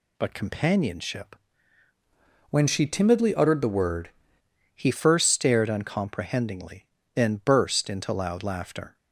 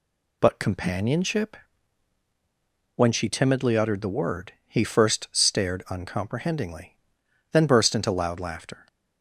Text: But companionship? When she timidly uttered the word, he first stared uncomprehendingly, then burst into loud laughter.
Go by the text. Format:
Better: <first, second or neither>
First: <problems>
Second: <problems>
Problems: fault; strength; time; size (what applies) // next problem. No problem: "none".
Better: second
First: changes voice from "When" to "word"; from 2.4 to 4.0 s; 1.6 s long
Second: none